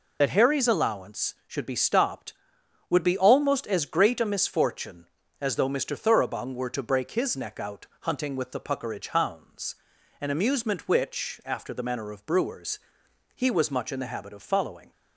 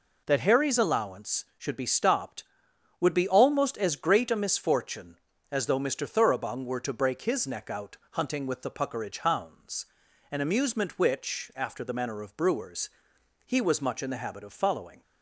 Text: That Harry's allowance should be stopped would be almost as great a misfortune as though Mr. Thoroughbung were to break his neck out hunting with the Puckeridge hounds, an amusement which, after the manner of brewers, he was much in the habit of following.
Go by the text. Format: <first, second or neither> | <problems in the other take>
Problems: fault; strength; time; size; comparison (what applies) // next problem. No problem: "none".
second | loses the start of "That"; at 0.2 s; 55 ms